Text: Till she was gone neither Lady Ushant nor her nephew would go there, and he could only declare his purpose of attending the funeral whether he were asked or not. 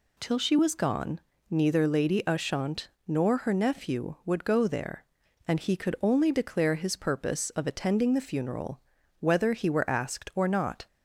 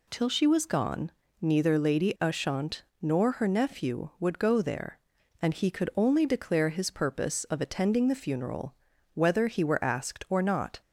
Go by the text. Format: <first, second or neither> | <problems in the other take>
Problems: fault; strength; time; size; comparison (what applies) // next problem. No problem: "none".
neither | pauses between "gone" and "neither"; slight; the same in both // pauses between "Ushant" and "nor"; slight; the same in both // pauses between "funeral" and "whether"; the same in both